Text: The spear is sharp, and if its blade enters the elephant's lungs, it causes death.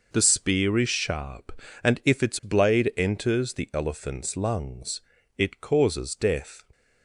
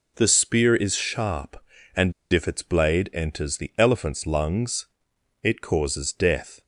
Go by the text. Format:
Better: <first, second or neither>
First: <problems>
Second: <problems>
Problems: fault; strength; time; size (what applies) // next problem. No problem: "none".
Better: first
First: none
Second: pauses between "and" and "if"; slight; at 2.1 s; 0.19 s long